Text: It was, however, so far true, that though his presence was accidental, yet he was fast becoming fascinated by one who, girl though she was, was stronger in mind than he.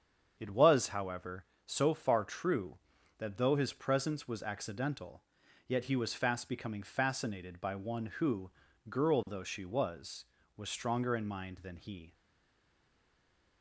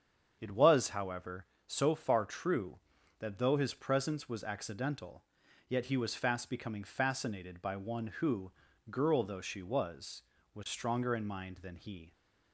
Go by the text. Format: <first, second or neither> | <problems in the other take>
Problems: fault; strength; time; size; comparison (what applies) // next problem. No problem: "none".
second | starts louder than the rest; strong; until 1.4 s; 7.5 dB; strong in the second // stays silent after the last word; noticeable; from 12.1 s on; 1.5 s long